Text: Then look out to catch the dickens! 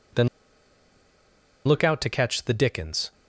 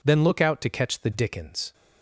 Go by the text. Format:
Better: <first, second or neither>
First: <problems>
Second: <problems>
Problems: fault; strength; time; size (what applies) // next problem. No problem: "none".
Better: second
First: pauses between "Then" and "look"; strong; at 0.2 s; 1.3 s long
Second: none